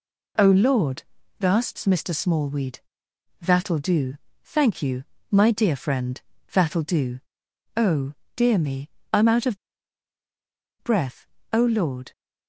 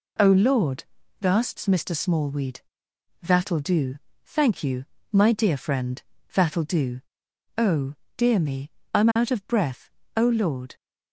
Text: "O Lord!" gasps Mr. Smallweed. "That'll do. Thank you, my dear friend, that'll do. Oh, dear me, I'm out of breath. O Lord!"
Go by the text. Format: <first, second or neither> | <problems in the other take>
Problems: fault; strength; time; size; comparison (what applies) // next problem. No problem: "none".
second | pauses between "of" and "breath"; strong; at 9.5 s; 1.2 s long